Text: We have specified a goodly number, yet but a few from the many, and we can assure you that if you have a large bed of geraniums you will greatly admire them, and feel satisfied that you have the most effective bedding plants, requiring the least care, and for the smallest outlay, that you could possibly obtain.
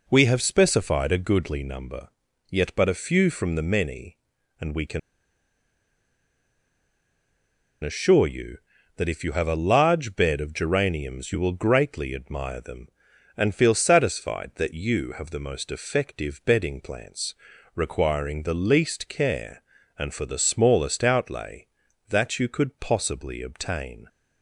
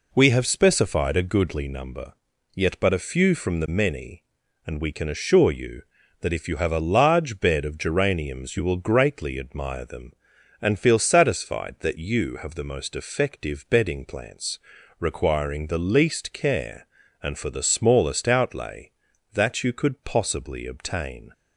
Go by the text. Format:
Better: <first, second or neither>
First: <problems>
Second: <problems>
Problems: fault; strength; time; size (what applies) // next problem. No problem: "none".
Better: second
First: pauses between "can" and "assure"; strong; at 4.9 s; 2.8 s long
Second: none